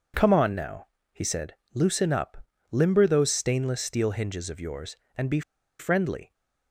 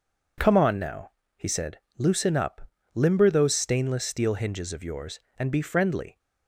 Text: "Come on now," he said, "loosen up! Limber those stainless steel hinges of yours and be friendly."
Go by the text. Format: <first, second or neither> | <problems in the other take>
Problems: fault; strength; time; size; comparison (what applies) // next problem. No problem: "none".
second | pauses between "be" and "friendly"; at 5.4 s; 0.38 s long